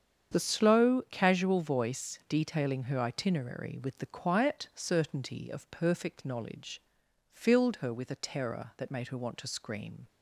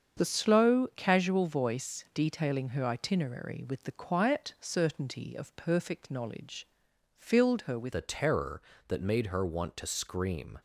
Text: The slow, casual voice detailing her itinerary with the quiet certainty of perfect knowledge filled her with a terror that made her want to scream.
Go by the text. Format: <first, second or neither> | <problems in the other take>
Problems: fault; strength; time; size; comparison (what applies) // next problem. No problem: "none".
first | starts louder than the rest; strong; until 1.2 s; 7 dB; strong in the first // pauses between "knowledge" and "filled"; noticeable; at 6.6 s; 0.54 s long; noticeable in the first // changes voice at "a"; from 7.9 s on; 2.6 s long